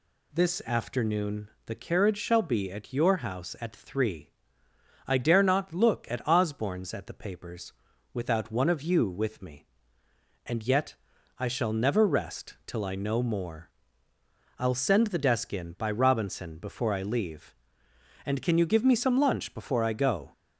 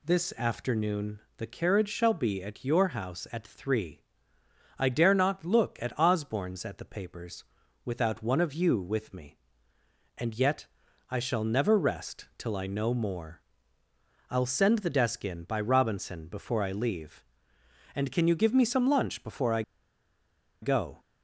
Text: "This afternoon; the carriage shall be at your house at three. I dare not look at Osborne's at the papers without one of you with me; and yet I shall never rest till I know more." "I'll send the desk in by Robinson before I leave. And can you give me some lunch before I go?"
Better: first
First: pauses between "papers" and "without"; at 7.7 s; 0.40 s long // pauses between "yet" and "I"; at 10.9 s; 0.42 s long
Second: pauses between "papers" and "without"; at 7.4 s; 0.40 s long // pauses between "yet" and "I"; at 10.6 s; 0.42 s long // pauses between "I" and "go"; at 19.6 s; 1.0 s long

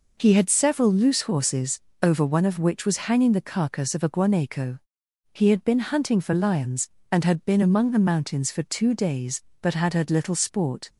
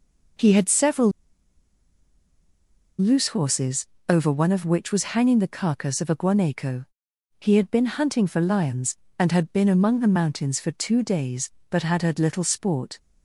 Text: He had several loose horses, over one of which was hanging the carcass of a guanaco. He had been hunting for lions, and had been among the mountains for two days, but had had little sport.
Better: first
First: none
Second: pauses between "several" and "loose"; strong; at 1.1 s; 1.8 s long

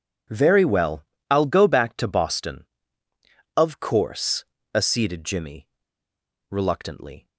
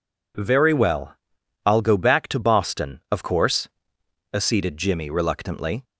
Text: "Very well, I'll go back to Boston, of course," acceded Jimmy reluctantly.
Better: second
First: pauses between "Jimmy" and "reluctantly"; noticeable; at 5.6 s; 0.82 s long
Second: none

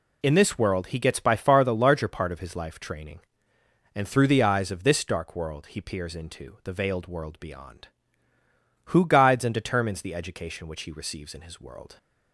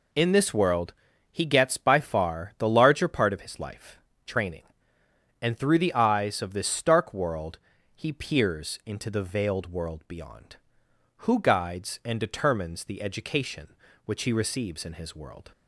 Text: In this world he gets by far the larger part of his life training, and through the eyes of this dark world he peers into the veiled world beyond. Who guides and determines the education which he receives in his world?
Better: first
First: none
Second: pauses between "world" and "he"; at 0.9 s; 0.38 s long // pauses between "life" and "training"; slight; at 3.9 s; 0.28 s long // says "stark" for "dark"; at 6.6 s // pauses between "world" and "he"; at 7.5 s; 0.38 s long

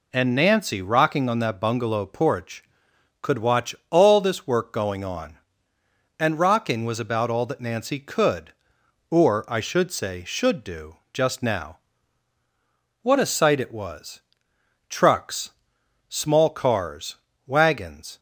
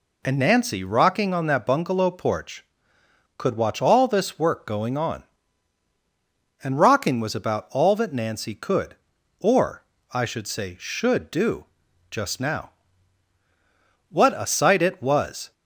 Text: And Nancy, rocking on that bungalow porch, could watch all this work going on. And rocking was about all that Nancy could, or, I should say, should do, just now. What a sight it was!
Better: second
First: goes on to say "Trucks small cars wagons"; strong; from 14.8 s on; 3.3 s long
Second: none

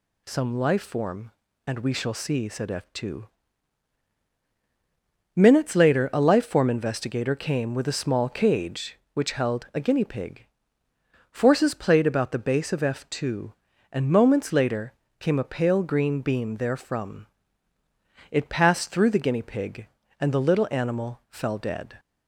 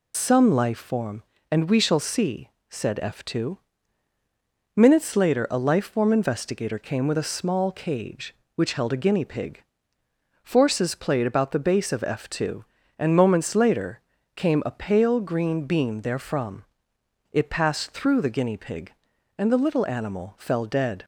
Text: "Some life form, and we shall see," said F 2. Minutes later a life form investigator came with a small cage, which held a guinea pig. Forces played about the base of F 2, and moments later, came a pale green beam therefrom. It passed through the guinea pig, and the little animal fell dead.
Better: first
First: none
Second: loses the start of "Some"; at 0.1 s; 90 ms

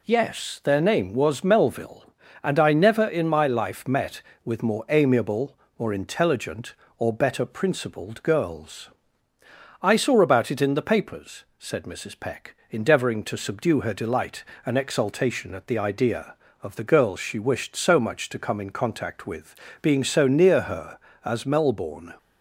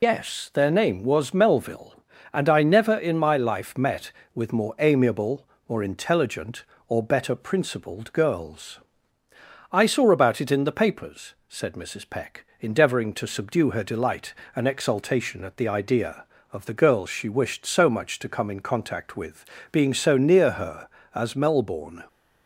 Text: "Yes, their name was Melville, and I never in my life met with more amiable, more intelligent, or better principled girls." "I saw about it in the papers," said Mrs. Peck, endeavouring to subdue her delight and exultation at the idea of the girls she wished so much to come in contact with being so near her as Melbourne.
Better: first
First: pauses between "with" and "being"; slight; at 19.5 s; 0.26 s long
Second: loses the start of "Yes"; at 0.0 s; 80 ms // pauses between "with" and "being"; slight; at 19.4 s; 0.26 s long

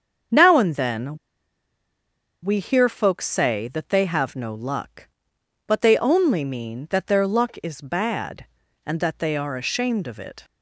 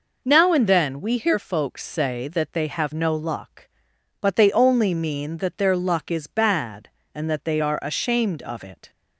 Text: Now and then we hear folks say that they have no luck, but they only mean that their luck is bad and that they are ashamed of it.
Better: second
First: starts louder than the rest; until 2.5 s; 7 dB // pauses between "then" and "we"; strong; at 1.1 s; 1.2 s long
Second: none

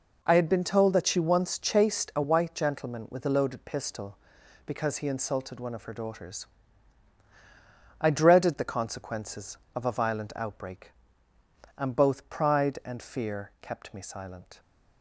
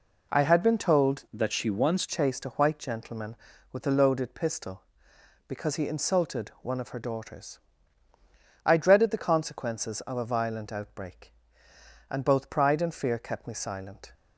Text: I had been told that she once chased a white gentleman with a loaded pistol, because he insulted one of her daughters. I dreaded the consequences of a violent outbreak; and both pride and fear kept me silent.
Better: first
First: none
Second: changes voice from "that" to "once"; from 1.3 to 2.0 s; 0.7 s long

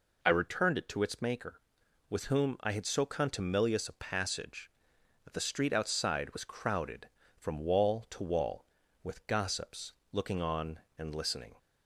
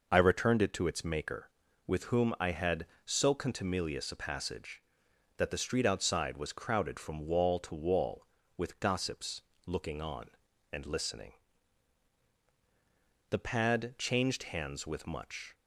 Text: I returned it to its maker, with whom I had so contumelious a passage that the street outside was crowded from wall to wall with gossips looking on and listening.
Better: first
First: pauses between "gossips" and "looking"; slight; at 9.9 s; 0.20 s long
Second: pauses between "gossips" and "looking"; slight; at 9.4 s; 0.24 s long // goes on to say "The pad changed hands with much"; strong; from 13.3 s on; 2.2 s long

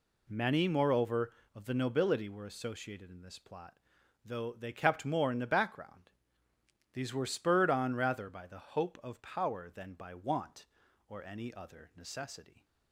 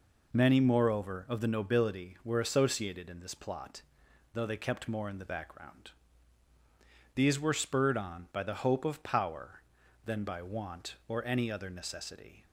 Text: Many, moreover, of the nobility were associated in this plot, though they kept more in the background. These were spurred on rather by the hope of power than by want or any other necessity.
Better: first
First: none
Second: skips "rather"; at 8.2 s

